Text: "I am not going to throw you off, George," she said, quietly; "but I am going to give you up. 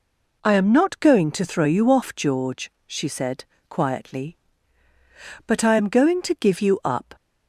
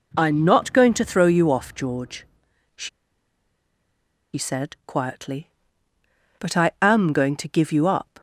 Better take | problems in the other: first | pauses between "she" and "said"; strong; at 2.8 s; 1.4 s long

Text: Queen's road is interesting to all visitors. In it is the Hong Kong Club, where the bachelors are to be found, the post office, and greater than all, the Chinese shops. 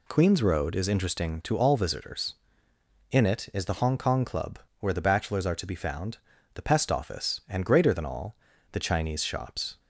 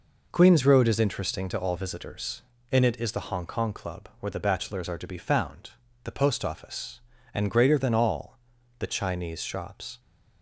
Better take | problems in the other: second | says "pest" for "post"; at 6.6 s

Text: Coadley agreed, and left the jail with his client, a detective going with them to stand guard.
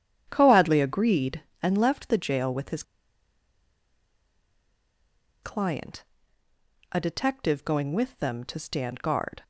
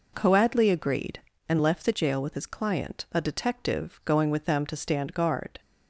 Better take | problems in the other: second | starts louder than the rest; strong; until 1.3 s; 9 dB // pauses between "his" and "client"; strong; at 2.8 s; 2.6 s long

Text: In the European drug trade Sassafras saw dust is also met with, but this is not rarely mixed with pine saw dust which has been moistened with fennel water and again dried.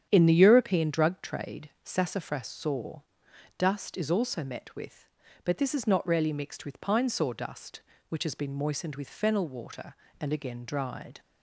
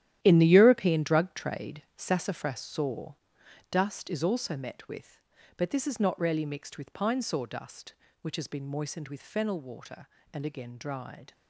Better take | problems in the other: first | gets quieter; strong; throughout; 12.5 dB // starts louder than the rest; strong; until 1.2 s; 12 dB; strong in the first // pauses between "trade" and "Sassafras"; slight; at 1.8 s; 0.16 s long; slight in the first // pauses between "saw" and "dust"; noticeable; at 3.1 s; 0.56 s long; noticeable in the first

